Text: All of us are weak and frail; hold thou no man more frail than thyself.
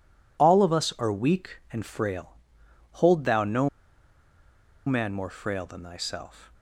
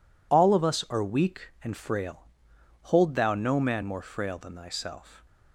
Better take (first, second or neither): second